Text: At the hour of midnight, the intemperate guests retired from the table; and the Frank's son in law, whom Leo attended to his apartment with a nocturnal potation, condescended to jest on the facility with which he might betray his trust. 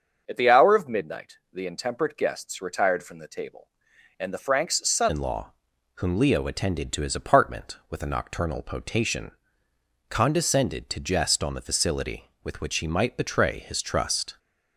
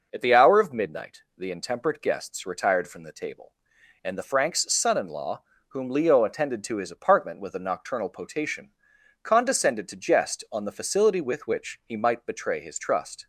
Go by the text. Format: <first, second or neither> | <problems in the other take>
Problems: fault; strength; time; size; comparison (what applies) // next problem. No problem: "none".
second | starts louder than the rest; until 1.2 s; 6.5 dB // changes voice at "in"; from 5.0 s on; 9.3 s long